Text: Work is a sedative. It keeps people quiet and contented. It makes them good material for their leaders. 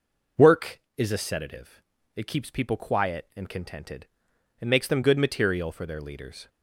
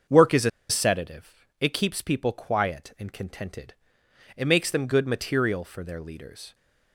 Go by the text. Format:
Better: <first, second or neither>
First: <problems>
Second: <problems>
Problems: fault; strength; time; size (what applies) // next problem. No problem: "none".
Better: first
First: none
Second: starts louder than the rest; until 1.3 s; 6.5 dB // pauses between "a" and "sedative"; slight; at 0.4 s; 0.20 s long